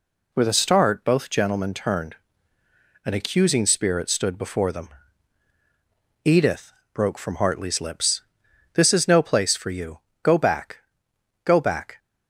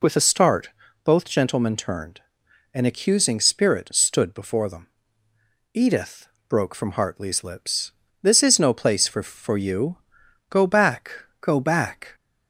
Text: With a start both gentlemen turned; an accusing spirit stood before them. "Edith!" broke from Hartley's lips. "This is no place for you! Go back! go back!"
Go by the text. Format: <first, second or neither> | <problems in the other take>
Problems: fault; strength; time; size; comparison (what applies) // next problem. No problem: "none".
first | pauses between "start" and "both"; slight; at 0.6 s; 0.36 s long // says "for" twice; at 9.2 s